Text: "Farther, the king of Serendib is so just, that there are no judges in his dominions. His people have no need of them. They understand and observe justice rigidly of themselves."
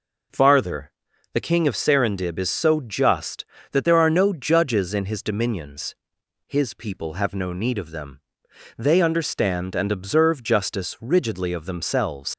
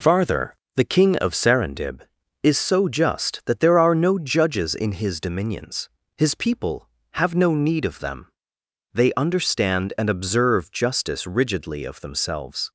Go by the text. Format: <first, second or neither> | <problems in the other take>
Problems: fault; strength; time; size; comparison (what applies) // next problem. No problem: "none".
second | leaves "themselves" unfinished; at 12.3 s; 95 ms